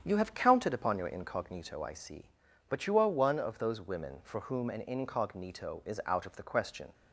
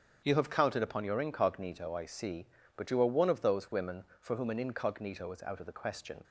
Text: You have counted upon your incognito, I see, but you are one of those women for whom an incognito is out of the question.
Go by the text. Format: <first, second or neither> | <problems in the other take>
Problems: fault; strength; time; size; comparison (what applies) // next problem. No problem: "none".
neither | starts louder than the rest; strong; the same in both